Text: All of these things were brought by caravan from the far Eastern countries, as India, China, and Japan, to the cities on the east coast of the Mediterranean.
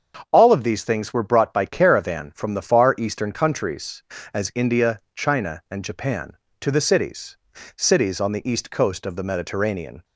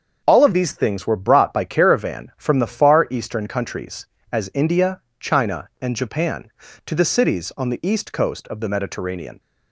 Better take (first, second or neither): second